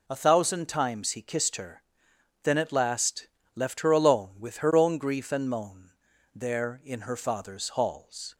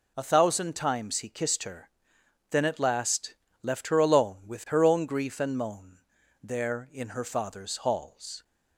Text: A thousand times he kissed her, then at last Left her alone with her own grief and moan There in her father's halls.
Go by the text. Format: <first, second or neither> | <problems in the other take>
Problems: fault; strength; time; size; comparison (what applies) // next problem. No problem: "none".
neither | pauses between "last" and "Left"; slight; the same in both // pauses between "moan" and "There"; the same in both